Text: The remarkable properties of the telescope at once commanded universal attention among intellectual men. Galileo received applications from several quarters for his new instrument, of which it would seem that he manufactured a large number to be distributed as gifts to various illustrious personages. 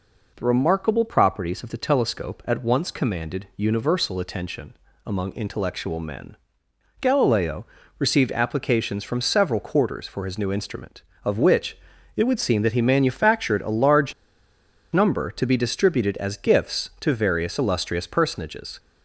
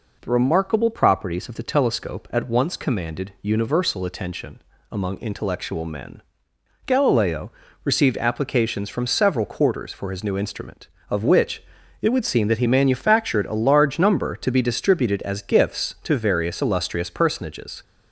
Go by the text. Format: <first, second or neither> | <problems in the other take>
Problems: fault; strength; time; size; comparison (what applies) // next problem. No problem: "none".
second | pauses between "attention" and "among"; slight; at 4.7 s; 0.32 s long; slight in the second // pauses between "Galileo" and "received"; slight; at 7.6 s; 0.34 s long; slight in the second // pauses between "which" and "it"; at 11.7 s; 0.38 s long; also in the second // pauses between "large" and "number"; noticeable; at 14.1 s; 0.81 s long